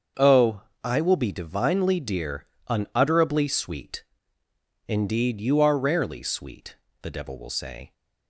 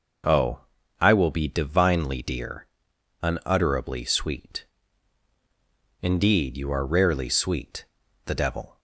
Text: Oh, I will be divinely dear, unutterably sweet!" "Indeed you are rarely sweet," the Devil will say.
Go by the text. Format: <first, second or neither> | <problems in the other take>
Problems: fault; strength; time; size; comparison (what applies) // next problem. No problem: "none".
first | starts louder than the rest; noticeable; until 1.6 s; 6 dB; also in the first // stops before "will say"; at 8.7 s